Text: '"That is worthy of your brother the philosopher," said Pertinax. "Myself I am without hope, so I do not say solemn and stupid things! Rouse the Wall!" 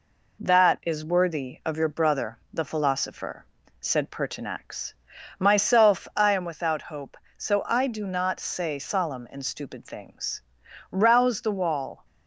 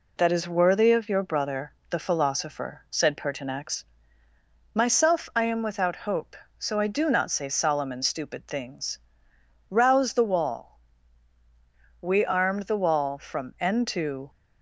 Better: first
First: none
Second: pauses between "brother" and "the"; slight; at 1.7 s; 0.16 s long // goes on to say "We armed the Wall from end to"; strong; from 11.9 s on; 2.3 s long

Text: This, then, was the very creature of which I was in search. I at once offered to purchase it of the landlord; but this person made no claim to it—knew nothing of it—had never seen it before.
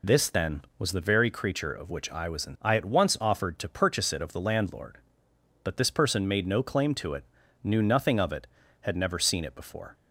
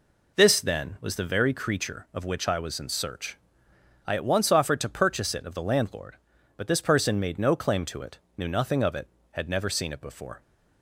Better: second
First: skips "search"; at 2.5 s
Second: none

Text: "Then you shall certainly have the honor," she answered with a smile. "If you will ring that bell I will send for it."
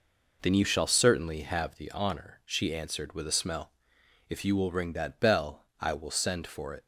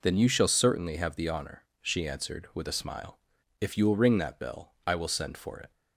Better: second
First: says "smell" for "smile"; at 3.3 s // pauses between "bell" and "I"; slight; at 5.6 s; 0.16 s long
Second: none

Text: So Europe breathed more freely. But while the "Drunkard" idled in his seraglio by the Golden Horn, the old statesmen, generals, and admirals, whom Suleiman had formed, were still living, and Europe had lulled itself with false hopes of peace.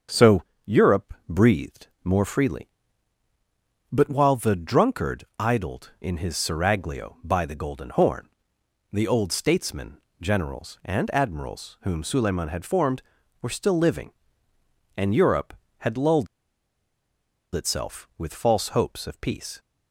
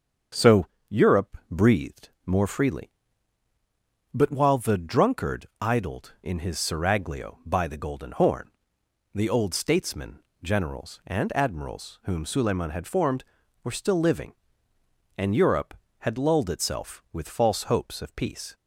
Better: second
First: starts louder than the rest; strong; until 1.5 s; 7.5 dB // pauses between "So" and "Europe"; slight; at 0.4 s; 0.24 s long // pauses between "breathed" and "more"; slight; at 1.8 s; 0.18 s long // pauses between "lulled" and "itself"; strong; at 16.2 s; 1.2 s long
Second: starts louder than the rest; strong; until 1.7 s; 7.5 dB // pauses between "So" and "Europe"; slight; at 0.6 s; 0.24 s long // pauses between "breathed" and "more"; slight; at 2.0 s; 0.18 s long

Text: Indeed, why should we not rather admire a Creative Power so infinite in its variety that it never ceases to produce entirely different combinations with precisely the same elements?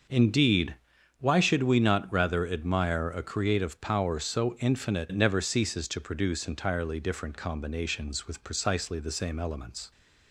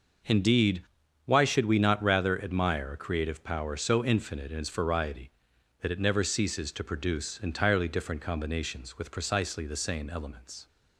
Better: second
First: starts louder than the rest; until 1.5 s; 6.5 dB // skips "in its variety that"; at 5.0 s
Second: none

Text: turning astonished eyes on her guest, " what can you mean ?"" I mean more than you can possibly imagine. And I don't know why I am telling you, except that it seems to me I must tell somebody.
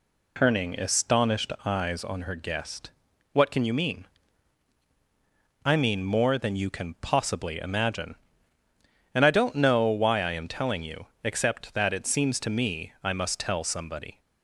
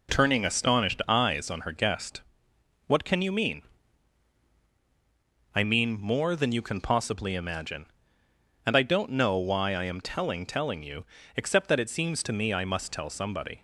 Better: first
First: none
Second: says "telling" twice; at 10.4 s

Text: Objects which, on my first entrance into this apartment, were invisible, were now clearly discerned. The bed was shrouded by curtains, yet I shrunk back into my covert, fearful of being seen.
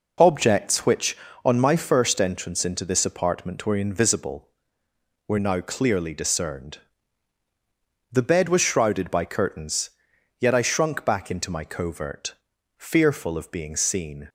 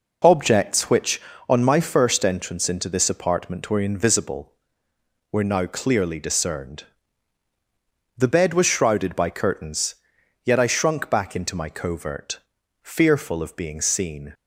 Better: neither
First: none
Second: none

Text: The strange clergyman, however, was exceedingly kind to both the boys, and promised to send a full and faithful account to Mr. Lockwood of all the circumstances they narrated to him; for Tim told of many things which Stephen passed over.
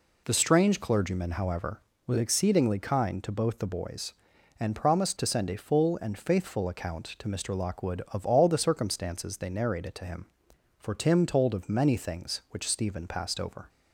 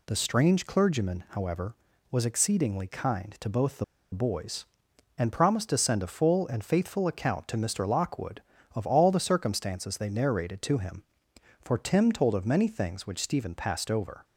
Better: first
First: none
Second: pauses between "the" and "boys"; slight; at 3.8 s; 0.29 s long

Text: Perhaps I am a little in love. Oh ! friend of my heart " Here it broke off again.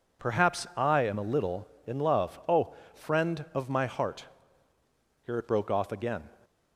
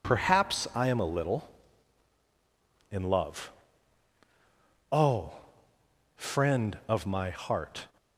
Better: first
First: none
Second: stops before "Here it broke off again"; at 7.9 s

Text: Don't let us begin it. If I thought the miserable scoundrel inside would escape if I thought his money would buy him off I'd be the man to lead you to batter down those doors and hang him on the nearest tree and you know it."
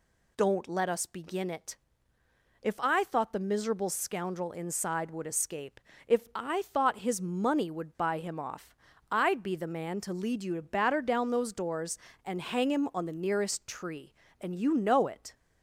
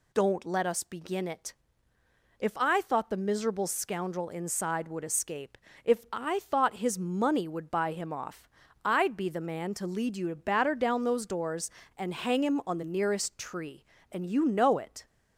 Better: neither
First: pauses between "escape" and "if"; slight; at 5.7 s; 0.28 s long // pauses between "off" and "I'd"; slight; at 8.7 s; 0.36 s long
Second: pauses between "escape" and "if"; slight; at 5.5 s; 0.28 s long // pauses between "off" and "I'd"; slight; at 8.4 s; 0.36 s long

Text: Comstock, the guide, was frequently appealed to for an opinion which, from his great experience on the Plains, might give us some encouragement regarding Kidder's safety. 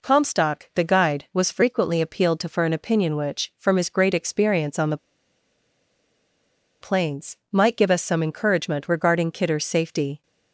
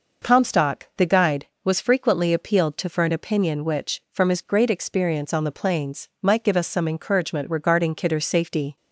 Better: second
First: pauses between "the" and "Plains"; strong; at 4.9 s; 1.8 s long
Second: none

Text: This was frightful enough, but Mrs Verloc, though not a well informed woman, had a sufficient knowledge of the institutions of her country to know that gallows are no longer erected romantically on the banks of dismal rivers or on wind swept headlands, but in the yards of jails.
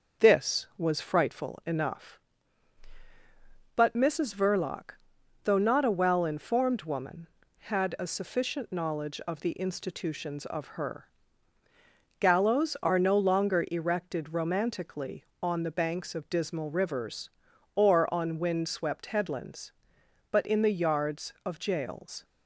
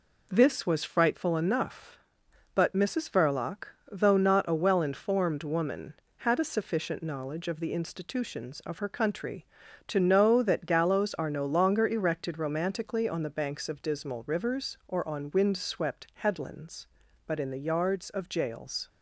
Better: second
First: starts louder than the rest; noticeable; until 1.3 s; 6 dB // skips "country to know that"; at 11.6 s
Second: none

